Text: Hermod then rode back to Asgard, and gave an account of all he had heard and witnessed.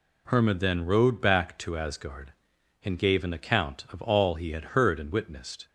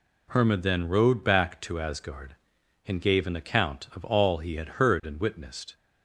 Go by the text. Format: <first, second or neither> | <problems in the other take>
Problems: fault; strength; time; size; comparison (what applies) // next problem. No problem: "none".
neither | none